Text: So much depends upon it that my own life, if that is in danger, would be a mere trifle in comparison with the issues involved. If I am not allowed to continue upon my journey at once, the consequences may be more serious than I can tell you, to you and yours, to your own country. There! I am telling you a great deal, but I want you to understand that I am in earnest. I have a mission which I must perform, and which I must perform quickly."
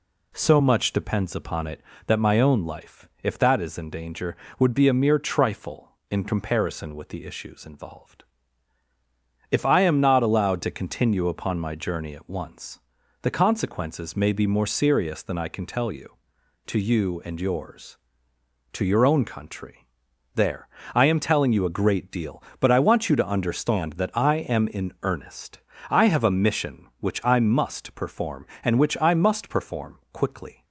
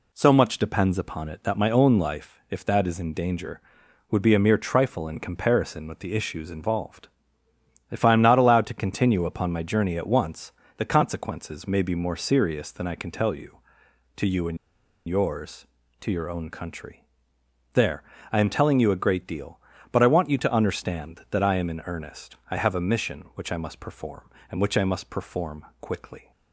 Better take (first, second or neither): first